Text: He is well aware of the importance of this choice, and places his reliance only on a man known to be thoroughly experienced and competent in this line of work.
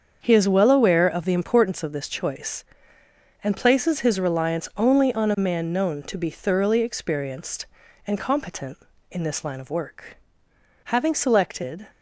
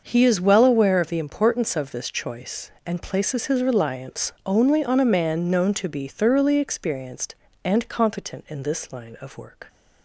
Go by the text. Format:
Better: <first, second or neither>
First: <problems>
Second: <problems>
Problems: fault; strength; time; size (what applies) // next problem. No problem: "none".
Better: second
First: starts louder than the rest; until 1.2 s; 7 dB // goes on to say "Having selected"; noticeable; from 10.8 s on; 1.0 s long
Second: starts louder than the rest; until 1.0 s; 6 dB